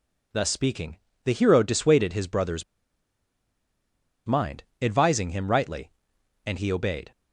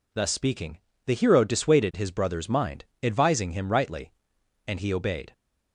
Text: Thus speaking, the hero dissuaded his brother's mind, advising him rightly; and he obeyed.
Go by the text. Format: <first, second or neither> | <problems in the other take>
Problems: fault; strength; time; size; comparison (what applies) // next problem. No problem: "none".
second | pauses between "brother's" and "mind"; strong; at 2.6 s; 1.6 s long